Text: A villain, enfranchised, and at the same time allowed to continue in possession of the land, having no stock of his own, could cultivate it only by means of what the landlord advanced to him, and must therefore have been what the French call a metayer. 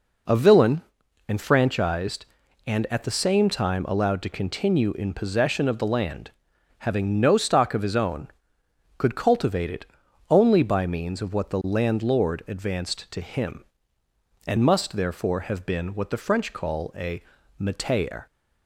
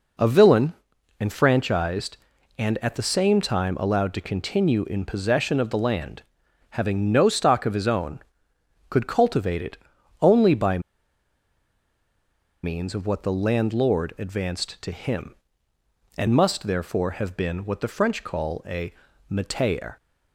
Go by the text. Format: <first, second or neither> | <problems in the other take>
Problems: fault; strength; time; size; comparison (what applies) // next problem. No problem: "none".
first | pauses between "it" and "only"; at 9.7 s; 0.42 s long; also in the first // pauses between "by" and "means"; strong; at 10.7 s; 1.8 s long // pauses between "a" and "metayer"; slight; at 18.9 s; 0.34 s long; slight in the first